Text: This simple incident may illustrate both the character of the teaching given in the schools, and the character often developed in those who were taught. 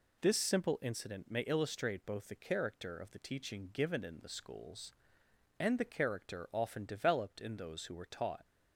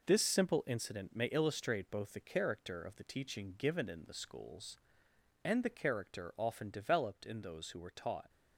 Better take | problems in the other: first | gets quieter; throughout; 6.5 dB

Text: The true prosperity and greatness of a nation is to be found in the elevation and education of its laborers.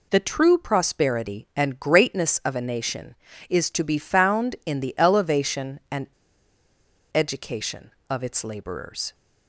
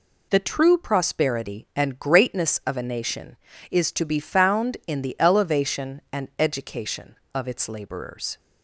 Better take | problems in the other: second | pauses between "and" and "education"; at 6.0 s; 1.0 s long

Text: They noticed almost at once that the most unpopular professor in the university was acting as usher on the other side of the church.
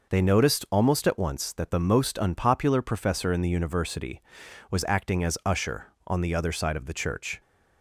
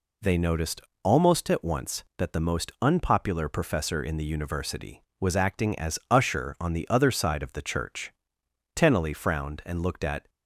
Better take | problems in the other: first | pauses between "noticed" and "almost"; slight; at 0.8 s; 0.22 s long // goes on to say "Tennelly frowned and looked at"; from 8.7 s on; 1.5 s long

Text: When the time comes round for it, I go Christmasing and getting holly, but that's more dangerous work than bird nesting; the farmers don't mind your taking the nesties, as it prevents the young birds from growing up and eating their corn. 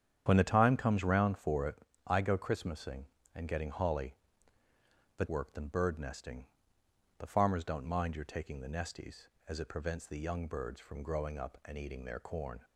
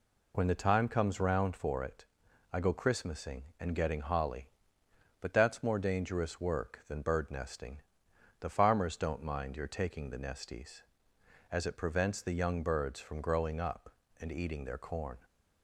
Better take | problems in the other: second | starts louder than the rest; strong; until 1.2 s; 9 dB // skips "that's more dangerous"; at 5.2 s

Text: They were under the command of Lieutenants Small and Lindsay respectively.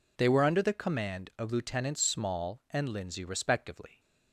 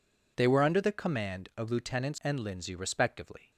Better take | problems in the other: first | skips "Small"; at 2.1 s

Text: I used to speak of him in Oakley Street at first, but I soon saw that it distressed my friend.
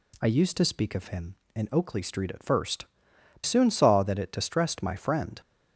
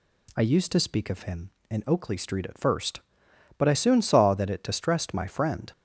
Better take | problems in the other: second | skips "but I"; at 3.1 s

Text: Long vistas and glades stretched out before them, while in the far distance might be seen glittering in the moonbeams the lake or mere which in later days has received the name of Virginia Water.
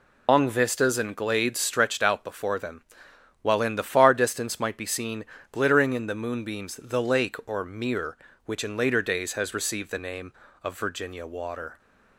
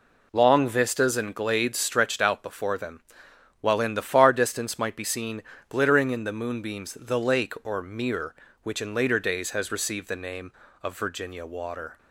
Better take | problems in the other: second | loses the start of "Long"; at 0.2 s; 165 ms // pauses between "seen" and "glittering"; slight; at 5.2 s; 0.28 s long; slight in the second

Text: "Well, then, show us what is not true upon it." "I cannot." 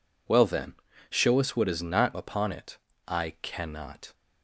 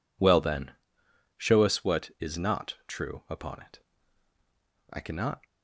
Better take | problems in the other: second | skips "true"; at 2.1 s

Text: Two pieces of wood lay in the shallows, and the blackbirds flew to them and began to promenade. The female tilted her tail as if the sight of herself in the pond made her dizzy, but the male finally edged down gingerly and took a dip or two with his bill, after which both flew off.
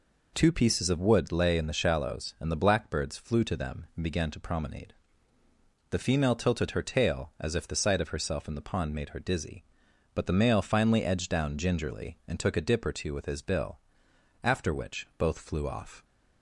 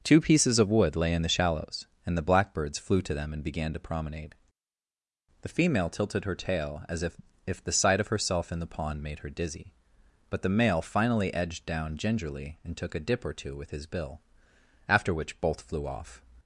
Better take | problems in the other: first | starts louder than the rest; until 1.0 s; 6.5 dB // says "if" twice; at 7.4 s

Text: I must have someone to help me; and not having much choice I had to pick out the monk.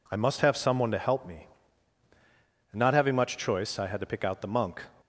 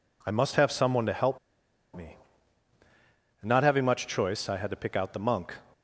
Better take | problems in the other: first | pauses between "help" and "me"; noticeable; at 1.3 s; 0.57 s long

